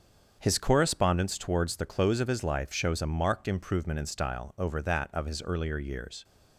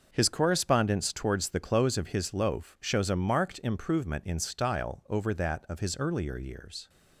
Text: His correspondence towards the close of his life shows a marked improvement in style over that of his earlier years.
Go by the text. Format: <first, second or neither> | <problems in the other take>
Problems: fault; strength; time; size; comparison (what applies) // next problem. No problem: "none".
first | starts louder than the rest; until 1.1 s; 6 dB; strong in the first // says "loaf" for "life"; at 2.3 s